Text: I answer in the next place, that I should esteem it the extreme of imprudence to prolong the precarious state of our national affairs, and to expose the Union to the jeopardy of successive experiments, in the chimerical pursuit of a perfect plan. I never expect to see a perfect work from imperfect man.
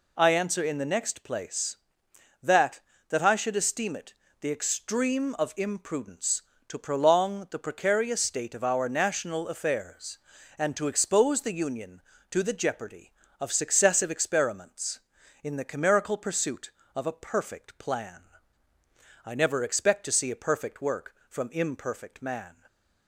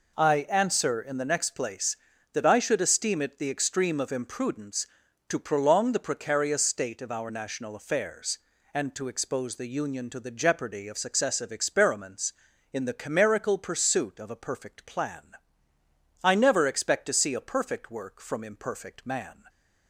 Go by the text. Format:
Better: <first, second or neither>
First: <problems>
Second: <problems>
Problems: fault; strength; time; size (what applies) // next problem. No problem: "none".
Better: second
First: says "that" twice; at 3.0 s // pauses between "it" and "the"; slight; at 4.1 s; 0.26 s long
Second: none